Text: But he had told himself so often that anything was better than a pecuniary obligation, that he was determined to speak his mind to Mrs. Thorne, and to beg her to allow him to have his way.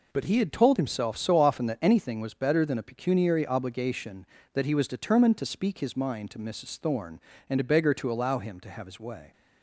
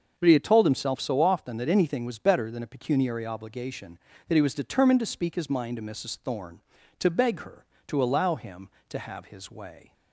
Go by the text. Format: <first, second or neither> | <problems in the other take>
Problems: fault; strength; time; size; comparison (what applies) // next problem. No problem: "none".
first | starts louder than the rest; until 1.1 s; 6.5 dB // skips "and"; at 6.7 s